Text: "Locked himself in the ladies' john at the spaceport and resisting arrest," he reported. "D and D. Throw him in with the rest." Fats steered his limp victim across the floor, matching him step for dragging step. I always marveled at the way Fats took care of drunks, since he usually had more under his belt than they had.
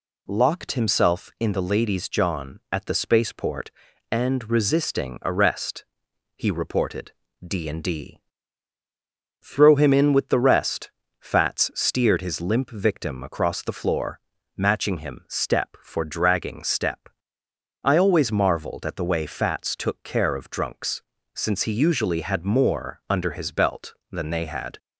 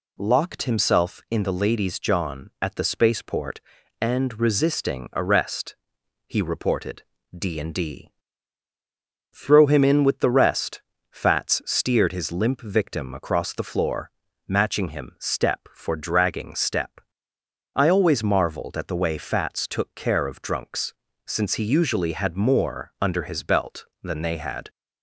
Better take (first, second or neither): neither